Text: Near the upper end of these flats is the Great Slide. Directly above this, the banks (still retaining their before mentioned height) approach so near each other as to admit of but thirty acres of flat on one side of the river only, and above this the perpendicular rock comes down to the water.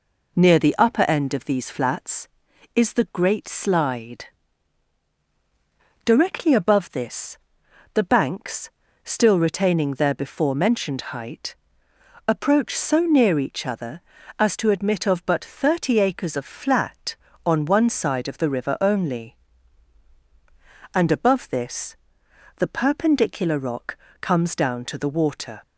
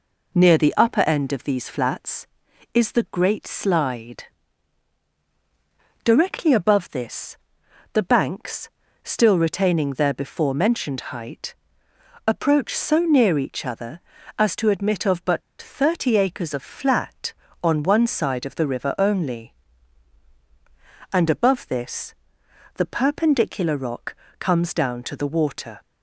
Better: first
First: pauses between "this" and "the"; noticeable; at 21.9 s; 0.62 s long // pauses between "rock" and "comes"; slight; at 23.9 s; 0.24 s long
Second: pauses between "but" and "thirty"; slight; at 15.4 s; 0.21 s long // pauses between "this" and "the"; noticeable; at 22.1 s; 0.62 s long // pauses between "rock" and "comes"; slight; at 24.1 s; 0.24 s long

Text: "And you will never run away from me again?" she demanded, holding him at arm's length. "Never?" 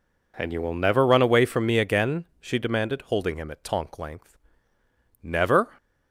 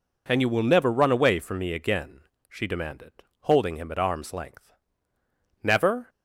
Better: second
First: says "tonk" for "arm's"; at 3.6 s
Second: none

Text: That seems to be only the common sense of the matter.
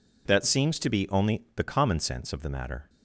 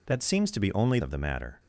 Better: first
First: none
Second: skips "the common sense"; at 1.0 s

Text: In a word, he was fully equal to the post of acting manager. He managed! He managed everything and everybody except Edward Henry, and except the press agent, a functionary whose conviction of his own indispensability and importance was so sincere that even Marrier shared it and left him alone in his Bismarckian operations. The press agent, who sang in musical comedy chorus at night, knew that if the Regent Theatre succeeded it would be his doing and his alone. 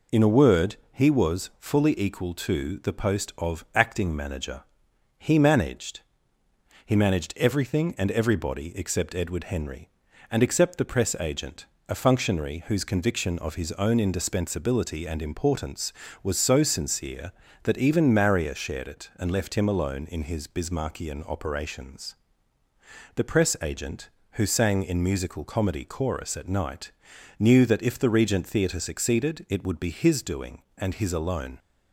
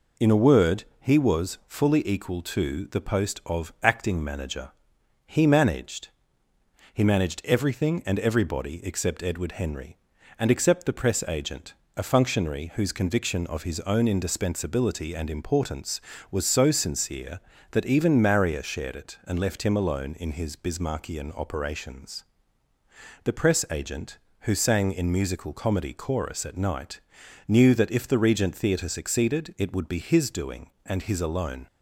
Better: neither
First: none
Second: none

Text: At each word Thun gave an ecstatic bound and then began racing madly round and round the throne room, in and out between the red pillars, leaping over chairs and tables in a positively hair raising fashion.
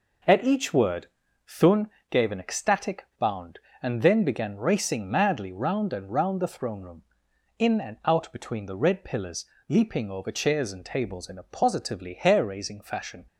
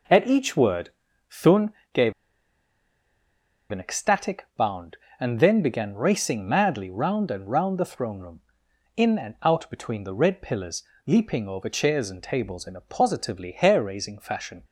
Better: first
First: pauses between "word" and "Thun"; at 1.0 s; 0.40 s long // pauses between "Thun" and "gave"; slight; at 1.8 s; 0.22 s long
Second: pauses between "word" and "Thun"; at 0.9 s; 0.40 s long // pauses between "Thun" and "gave"; slight; at 1.7 s; 0.22 s long // pauses between "gave" and "an"; strong; at 2.1 s; 1.5 s long

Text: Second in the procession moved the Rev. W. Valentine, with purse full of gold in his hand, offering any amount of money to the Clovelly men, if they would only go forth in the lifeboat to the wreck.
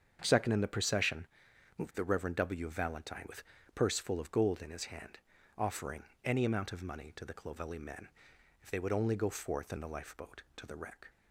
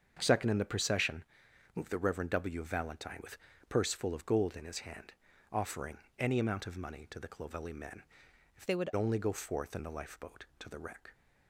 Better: first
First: starts louder than the rest; strong; until 1.2 s; 7.5 dB // pauses between "procession" and "moved"; noticeable; at 1.2 s; 0.52 s long // pauses between "with" and "purse"; slight; at 3.4 s; 0.32 s long // pauses between "offering" and "any"; slight; at 6.0 s; 0.20 s long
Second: starts louder than the rest; strong; until 1.2 s; 7 dB // pauses between "procession" and "moved"; noticeable; at 1.2 s; 0.52 s long // pauses between "with" and "purse"; slight; at 3.3 s; 0.32 s long // pauses between "offering" and "any"; slight; at 5.9 s; 0.20 s long // changes voice from "they" to "would"; from 8.6 to 8.8 s; 0.2 s long

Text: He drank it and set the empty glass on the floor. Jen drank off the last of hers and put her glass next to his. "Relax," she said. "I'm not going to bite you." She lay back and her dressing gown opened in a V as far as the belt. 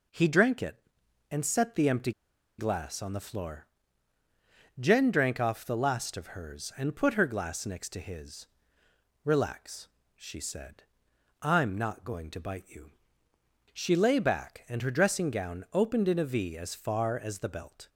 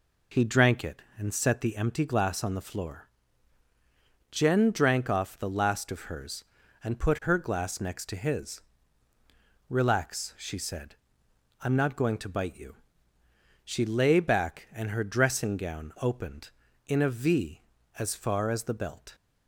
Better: second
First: pauses between "empty" and "glass"; noticeable; at 2.1 s; 0.47 s long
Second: none

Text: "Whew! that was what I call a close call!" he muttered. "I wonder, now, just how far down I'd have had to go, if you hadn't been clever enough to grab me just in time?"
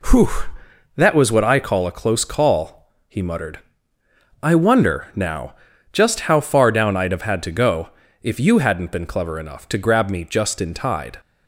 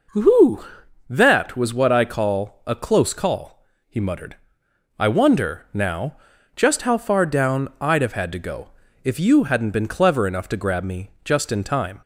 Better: second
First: says "tide" for "time"; at 10.7 s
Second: none

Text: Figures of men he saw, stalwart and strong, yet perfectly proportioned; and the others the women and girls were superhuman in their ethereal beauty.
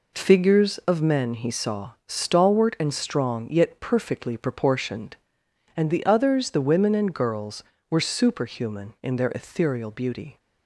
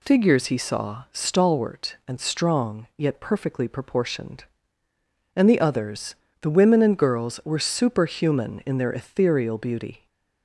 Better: first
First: none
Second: skips "of men"; at 0.4 s // pauses between "others" and "the"; slight; at 6.1 s; 0.26 s long

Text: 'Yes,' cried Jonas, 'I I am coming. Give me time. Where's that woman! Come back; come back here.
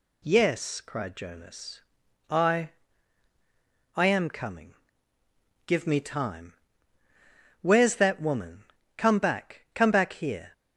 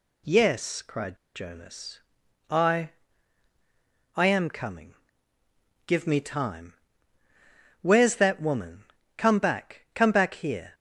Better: first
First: pauses between "I" and "I"; strong; at 2.6 s; 1.2 s long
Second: pauses between "cried" and "Jonas"; slight; at 1.1 s; 0.18 s long // pauses between "I" and "I"; strong; at 2.8 s; 1.2 s long

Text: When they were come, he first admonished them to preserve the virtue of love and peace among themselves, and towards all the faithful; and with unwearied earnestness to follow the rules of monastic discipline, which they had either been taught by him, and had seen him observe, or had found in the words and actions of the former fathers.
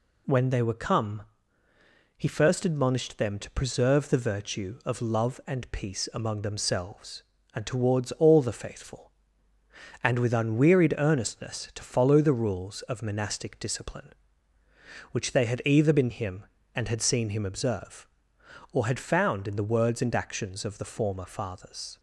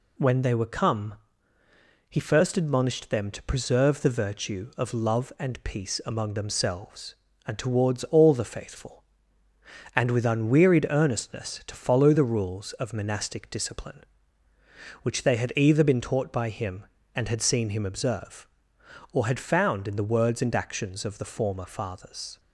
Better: second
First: skips "taught by"; at 16.0 s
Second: none

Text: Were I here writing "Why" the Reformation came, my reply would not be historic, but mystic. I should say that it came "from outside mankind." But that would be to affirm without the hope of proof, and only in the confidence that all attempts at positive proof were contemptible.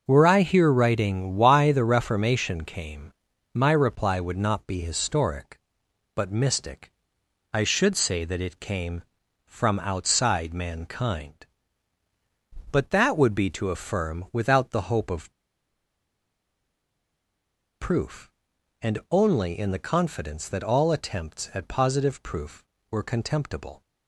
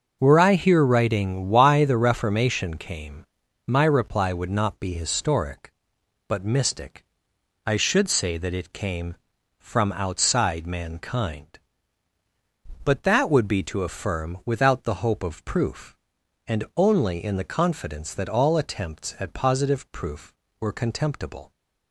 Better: second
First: starts louder than the rest; until 1.0 s; 6 dB // pauses between "of" and "proof"; strong; at 15.3 s; 2.4 s long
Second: starts louder than the rest; until 1.2 s; 6 dB

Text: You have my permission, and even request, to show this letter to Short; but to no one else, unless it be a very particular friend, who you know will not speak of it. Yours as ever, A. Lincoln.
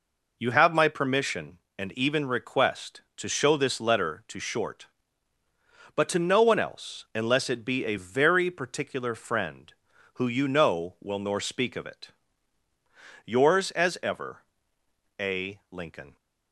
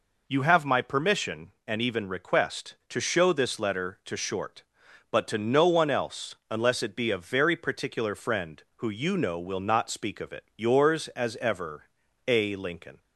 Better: second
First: says "nor" for "not"; at 11.1 s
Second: none

